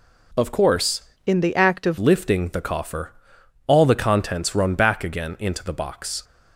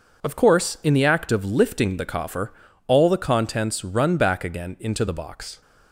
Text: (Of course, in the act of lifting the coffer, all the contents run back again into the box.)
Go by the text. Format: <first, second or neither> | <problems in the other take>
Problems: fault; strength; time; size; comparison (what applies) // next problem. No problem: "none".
second | changes voice from "in" to "of"; from 1.2 to 1.9 s; 0.7 s long